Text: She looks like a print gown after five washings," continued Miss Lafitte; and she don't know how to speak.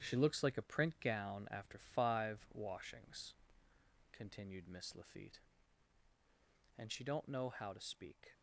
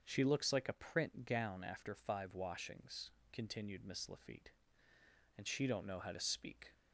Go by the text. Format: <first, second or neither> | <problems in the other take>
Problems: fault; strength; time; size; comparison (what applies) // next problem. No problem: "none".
second | gets quieter; strong; throughout; 8.5 dB // starts louder than the rest; strong; until 1.0 s; 9 dB; also in the second